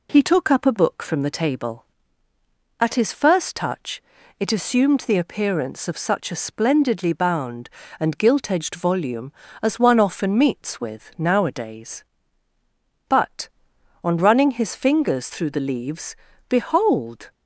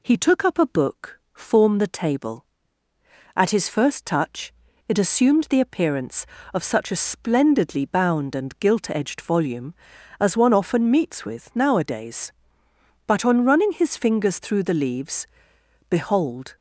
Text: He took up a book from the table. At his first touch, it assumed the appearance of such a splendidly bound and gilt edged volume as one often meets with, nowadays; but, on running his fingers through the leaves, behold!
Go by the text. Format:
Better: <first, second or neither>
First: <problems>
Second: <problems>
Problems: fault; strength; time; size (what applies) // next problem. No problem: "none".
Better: first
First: none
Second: says "form" for "from"; at 1.3 s